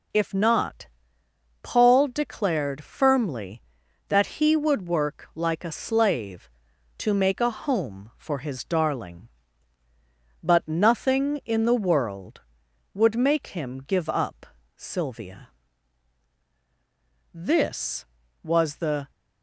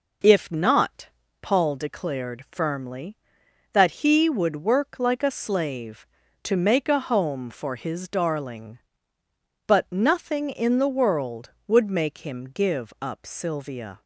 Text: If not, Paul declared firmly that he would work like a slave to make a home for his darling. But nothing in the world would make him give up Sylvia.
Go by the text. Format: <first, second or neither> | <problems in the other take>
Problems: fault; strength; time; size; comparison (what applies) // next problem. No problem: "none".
second | pauses between "up" and "Sylvia"; slight; at 14.4 s; 0.30 s long // goes on to say "This was the"; strong; from 17.3 s on; 1.7 s long